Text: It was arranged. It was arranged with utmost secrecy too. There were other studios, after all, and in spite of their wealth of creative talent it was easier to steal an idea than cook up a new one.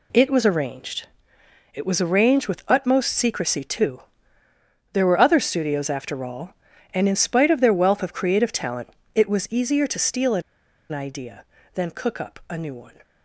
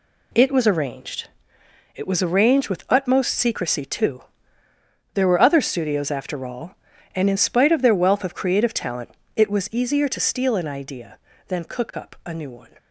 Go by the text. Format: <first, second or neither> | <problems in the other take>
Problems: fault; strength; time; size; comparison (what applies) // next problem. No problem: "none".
second | pauses between "talent" and "it"; slight; at 8.8 s; 0.26 s long; slight in the second // pauses between "an" and "idea"; noticeable; at 10.4 s; 0.50 s long